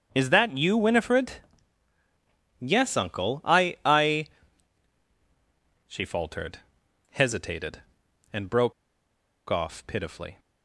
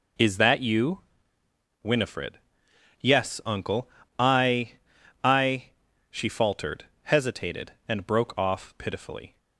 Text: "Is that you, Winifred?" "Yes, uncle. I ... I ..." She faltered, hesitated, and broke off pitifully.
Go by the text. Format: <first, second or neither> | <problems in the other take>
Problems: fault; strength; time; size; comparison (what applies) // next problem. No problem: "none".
second | starts louder than the rest; strong; until 1.1 s; 8 dB // pauses between "broke" and "off"; noticeable; at 8.7 s; 0.76 s long